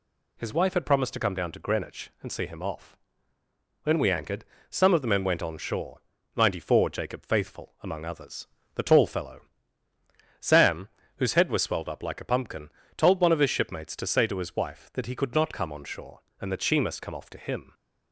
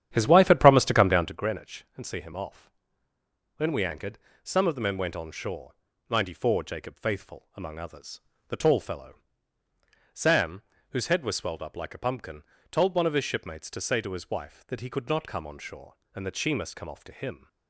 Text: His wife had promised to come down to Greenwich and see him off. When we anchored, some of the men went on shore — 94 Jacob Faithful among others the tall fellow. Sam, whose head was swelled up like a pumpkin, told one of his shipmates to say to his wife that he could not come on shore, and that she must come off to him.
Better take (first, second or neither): first